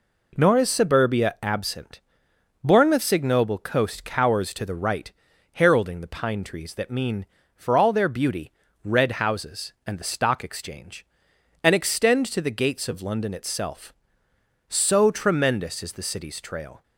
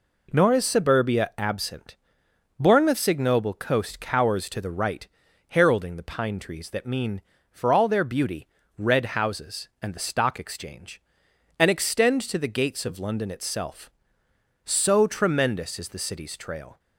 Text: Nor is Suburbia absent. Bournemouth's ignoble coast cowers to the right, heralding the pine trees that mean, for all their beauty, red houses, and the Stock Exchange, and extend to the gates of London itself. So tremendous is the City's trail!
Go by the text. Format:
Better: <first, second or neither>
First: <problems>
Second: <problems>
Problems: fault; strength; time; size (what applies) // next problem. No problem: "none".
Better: neither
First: none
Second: none